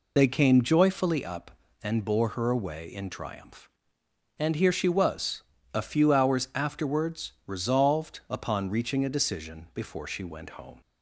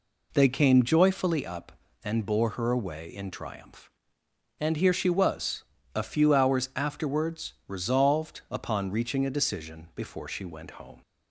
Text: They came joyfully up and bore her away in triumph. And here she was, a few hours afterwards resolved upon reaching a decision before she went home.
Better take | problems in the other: second | loses the start of "They"; at 0.1 s; 60 ms

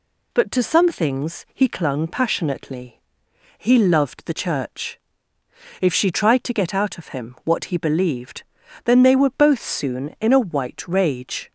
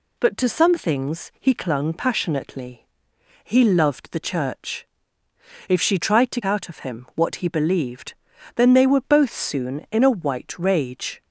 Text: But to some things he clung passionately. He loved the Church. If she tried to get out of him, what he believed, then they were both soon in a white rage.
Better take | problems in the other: first | skips "get"; at 6.4 s

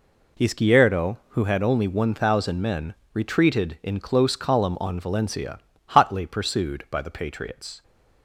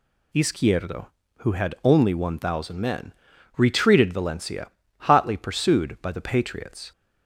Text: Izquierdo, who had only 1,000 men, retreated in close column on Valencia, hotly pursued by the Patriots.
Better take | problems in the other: first | skips "in close column on"; at 4.1 s

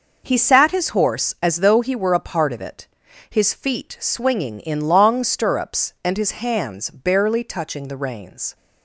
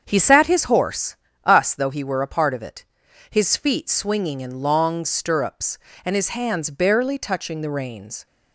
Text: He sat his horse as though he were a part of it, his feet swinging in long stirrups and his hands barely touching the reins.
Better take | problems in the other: first | starts louder than the rest; strong; until 1.0 s; 7.5 dB // says "us" for "as"; at 1.4 s

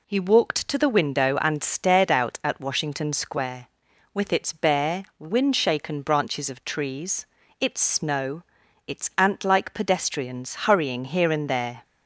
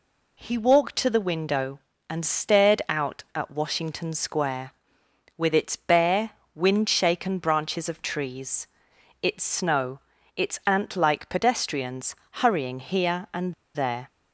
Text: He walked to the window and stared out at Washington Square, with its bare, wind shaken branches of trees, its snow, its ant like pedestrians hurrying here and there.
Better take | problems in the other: first | pauses between "pedestrians" and "hurrying"; slight; at 12.1 s; 0.18 s long // pauses between "and" and "there"; slight; at 13.5 s; 0.21 s long

